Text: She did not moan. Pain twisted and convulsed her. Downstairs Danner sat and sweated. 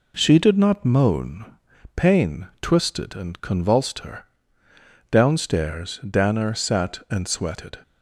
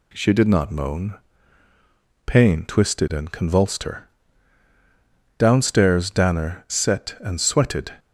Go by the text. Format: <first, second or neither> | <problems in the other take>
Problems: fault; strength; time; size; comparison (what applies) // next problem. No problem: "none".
first | says "set" for "sat"; at 6.6 s